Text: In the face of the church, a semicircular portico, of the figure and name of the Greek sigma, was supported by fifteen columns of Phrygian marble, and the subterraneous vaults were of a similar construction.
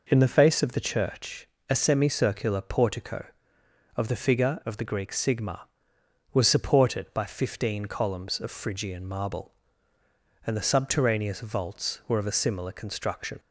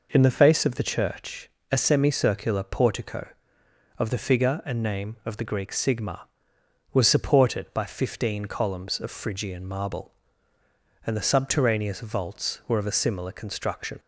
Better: second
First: skips "and name"; at 4.6 s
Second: none

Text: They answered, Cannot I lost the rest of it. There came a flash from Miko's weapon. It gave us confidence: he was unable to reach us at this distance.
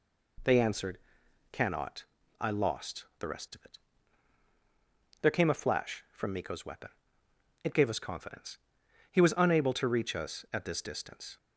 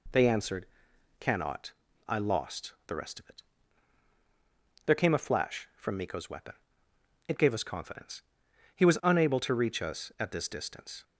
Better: neither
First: pauses between "Cannot" and "I"; slight; at 2.0 s; 0.34 s long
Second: pauses between "Cannot" and "I"; slight; at 1.7 s; 0.34 s long

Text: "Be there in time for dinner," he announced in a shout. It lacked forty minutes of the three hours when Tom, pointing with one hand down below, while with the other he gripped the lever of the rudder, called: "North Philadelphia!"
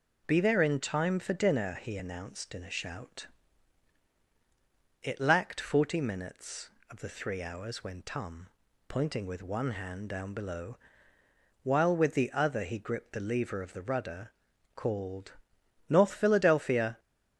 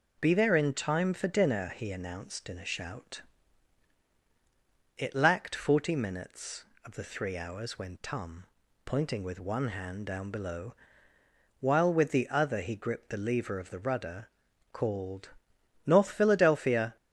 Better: neither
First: none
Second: none

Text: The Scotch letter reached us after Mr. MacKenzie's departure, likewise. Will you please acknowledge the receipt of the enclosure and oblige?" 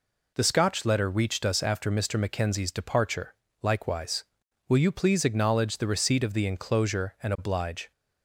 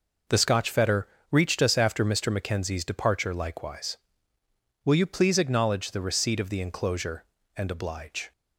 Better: first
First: none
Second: says "fetter" for "letter"; at 0.6 s

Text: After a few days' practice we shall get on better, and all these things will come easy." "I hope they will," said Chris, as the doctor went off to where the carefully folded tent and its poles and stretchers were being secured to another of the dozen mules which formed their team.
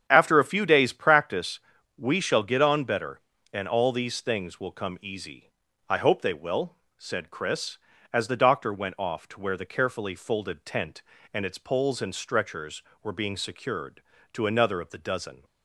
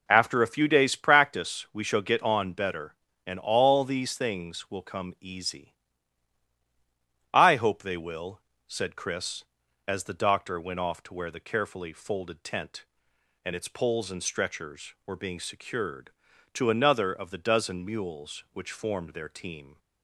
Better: second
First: starts louder than the rest; strong; until 1.1 s; 8.5 dB // pauses between "practice" and "we"; at 1.5 s; 0.38 s long // stops before "mules which formed their team"; at 15.4 s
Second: none

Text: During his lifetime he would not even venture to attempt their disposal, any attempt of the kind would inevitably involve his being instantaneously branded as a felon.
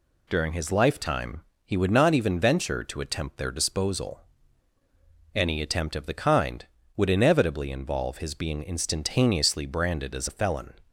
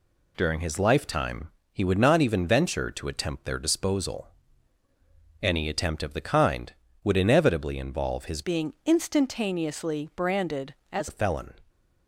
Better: first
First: pauses between "lifetime" and "he"; slight; at 1.4 s; 0.22 s long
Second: pauses between "lifetime" and "he"; slight; at 1.4 s; 0.22 s long // changes voice from "being" to "as"; from 8.4 to 11.0 s; 2.6 s long

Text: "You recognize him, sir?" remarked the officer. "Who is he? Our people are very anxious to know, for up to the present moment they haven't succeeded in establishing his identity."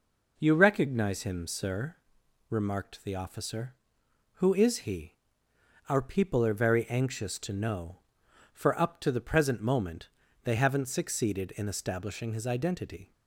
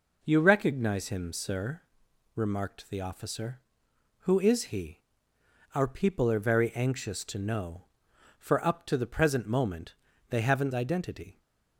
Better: first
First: pauses between "moment" and "they"; slight; at 10.0 s; 0.34 s long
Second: pauses between "moment" and "they"; slight; at 9.9 s; 0.34 s long // skips "succeeded in establishing his"; at 10.7 s

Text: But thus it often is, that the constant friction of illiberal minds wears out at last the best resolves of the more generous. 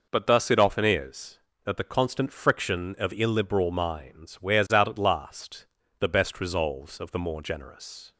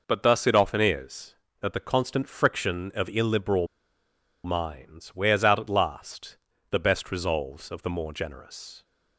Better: first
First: pauses between "last" and "the"; slight; at 5.6 s; 0.34 s long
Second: pauses between "illiberal" and "minds"; noticeable; at 3.6 s; 0.78 s long // pauses between "last" and "the"; slight; at 6.3 s; 0.34 s long

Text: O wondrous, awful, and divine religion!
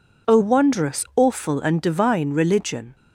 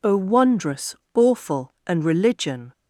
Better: first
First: none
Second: skips "divine"; at 2.0 s

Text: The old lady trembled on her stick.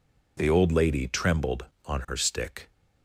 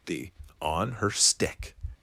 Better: first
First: none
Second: skips "old lady trembled"; at 0.4 s

